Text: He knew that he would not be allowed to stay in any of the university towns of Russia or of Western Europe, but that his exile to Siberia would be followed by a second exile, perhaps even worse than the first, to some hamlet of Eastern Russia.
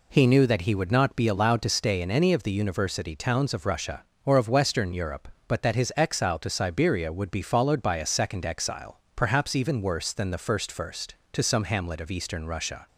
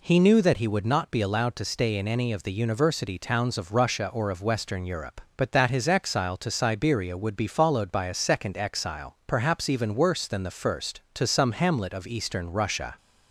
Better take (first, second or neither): second